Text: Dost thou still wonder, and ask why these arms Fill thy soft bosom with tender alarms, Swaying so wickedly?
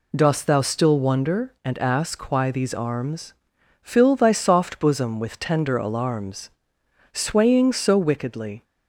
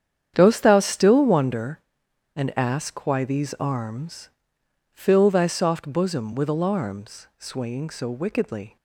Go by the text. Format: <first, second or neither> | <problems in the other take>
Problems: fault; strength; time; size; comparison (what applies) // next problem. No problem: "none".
first | starts louder than the rest; strong; until 1.3 s; 8.5 dB // pauses between "arms" and "Fill"; noticeable; at 4.2 s; 0.62 s long; noticeable in the first // skips "tender"; at 6.4 s